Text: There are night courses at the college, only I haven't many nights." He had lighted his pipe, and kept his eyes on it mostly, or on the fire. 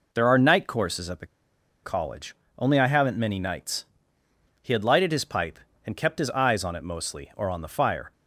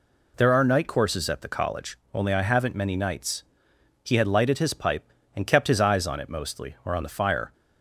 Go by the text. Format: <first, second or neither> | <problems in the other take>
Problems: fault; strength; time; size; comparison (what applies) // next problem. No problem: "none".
second | pauses between "the" and "college"; noticeable; at 1.2 s; 0.57 s long